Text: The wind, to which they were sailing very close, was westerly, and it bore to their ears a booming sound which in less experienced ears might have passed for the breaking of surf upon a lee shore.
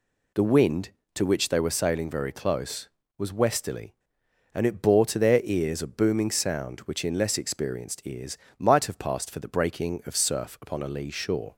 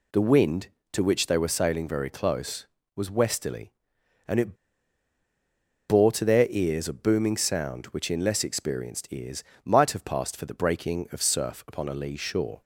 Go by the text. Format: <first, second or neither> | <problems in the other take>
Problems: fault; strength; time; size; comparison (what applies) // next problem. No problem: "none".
first | pauses between "it" and "bore"; strong; at 4.5 s; 1.3 s long // pauses between "ears" and "might"; slight; at 9.4 s; 0.22 s long; slight in the first